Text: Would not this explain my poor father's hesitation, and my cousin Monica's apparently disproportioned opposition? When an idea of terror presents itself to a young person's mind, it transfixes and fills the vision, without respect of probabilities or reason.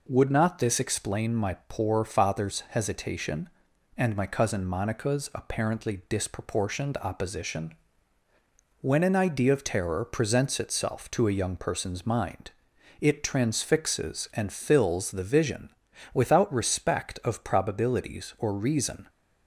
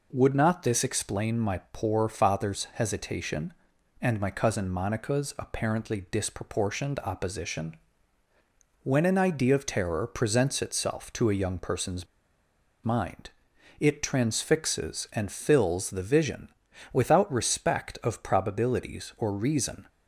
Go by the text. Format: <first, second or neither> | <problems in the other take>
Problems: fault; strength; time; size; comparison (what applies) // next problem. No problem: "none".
first | pauses between "person's" and "mind"; noticeable; at 12.0 s; 0.79 s long